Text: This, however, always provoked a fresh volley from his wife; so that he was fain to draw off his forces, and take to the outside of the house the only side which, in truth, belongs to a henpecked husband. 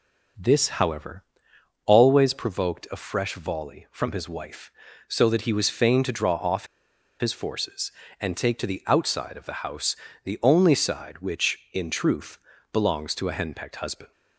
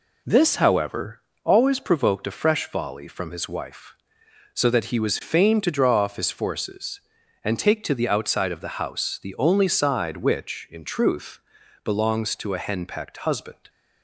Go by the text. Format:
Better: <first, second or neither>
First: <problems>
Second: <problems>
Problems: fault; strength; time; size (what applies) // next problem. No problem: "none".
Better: second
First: pauses between "off" and "his"; noticeable; at 6.6 s; 0.54 s long // pauses between "house" and "the"; slight; at 9.9 s; 0.26 s long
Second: none